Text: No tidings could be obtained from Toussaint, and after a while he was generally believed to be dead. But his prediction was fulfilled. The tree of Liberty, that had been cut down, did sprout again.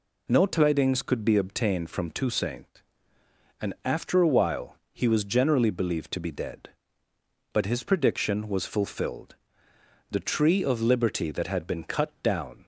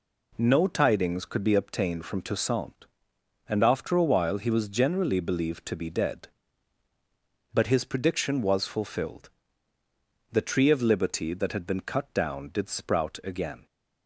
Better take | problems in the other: second | pauses between "while" and "he"; slight; at 4.7 s; 0.16 s long // stops before "did sprout again"; at 12.6 s

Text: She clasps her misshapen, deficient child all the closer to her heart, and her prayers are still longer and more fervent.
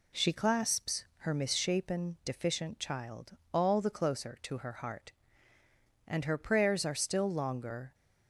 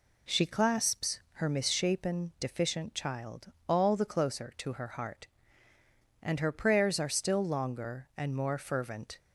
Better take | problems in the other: second | pauses between "child" and "all"; slight; at 3.3 s; 0.16 s long; slight in the second // stops before "and more fervent"; at 7.9 s

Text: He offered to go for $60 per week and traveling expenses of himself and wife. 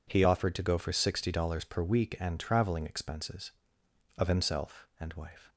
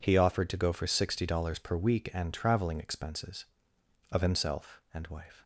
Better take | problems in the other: neither | none

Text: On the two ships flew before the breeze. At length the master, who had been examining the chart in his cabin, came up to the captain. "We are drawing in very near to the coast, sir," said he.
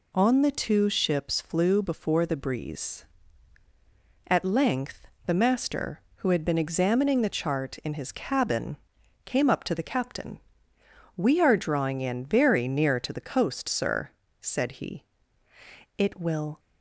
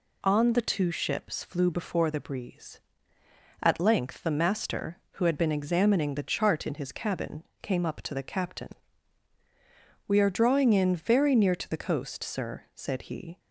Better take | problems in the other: second | pauses between "length" and "the"; slight; at 5.0 s; 0.22 s long // goes on to say "It will"; from 15.9 s on; 0.60 s long

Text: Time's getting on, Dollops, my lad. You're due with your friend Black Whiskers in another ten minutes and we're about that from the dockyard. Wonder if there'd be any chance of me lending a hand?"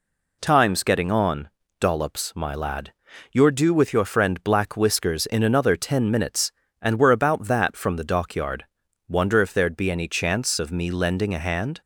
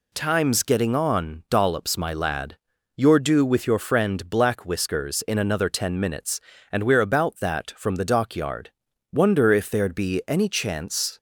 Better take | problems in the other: first | stops before "of me lending a hand"; at 11.1 s

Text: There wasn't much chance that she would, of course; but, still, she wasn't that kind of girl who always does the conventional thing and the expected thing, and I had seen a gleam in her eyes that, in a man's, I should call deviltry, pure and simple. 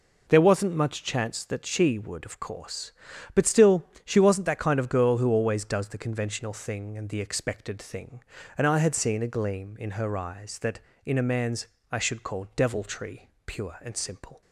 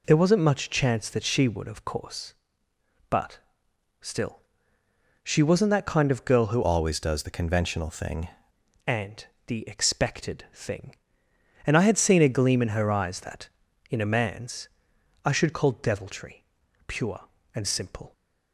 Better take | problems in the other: first | changes voice from "always" to "thing"; from 6.6 to 8.2 s; 1.6 s long // pauses between "and" and "the"; slight; at 9.2 s; 0.22 s long

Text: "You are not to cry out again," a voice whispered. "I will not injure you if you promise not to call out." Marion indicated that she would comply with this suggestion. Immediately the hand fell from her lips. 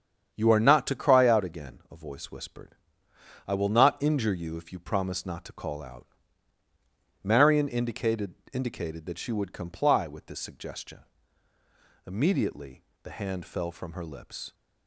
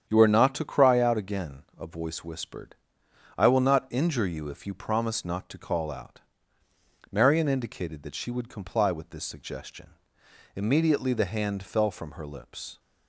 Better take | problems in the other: second | starts louder than the rest; strong; until 1.3 s; 8 dB; strong in the second // says "indicated" twice; at 8.5 s // pauses between "Immediately" and "the"; slight; at 12.8 s; 0.22 s long

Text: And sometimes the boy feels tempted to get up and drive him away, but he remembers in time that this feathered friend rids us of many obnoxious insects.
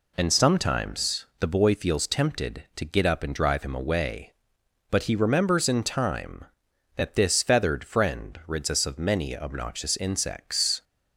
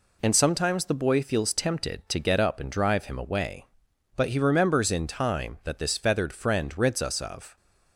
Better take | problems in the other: first | stops before "many obnoxious insects"; at 7.5 s

